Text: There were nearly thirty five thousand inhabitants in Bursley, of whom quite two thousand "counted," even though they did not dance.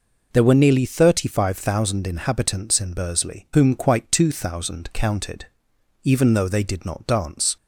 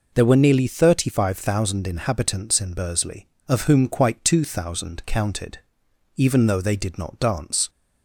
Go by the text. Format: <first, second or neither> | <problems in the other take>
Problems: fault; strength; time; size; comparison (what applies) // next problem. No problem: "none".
second | skips "of"; at 3.4 s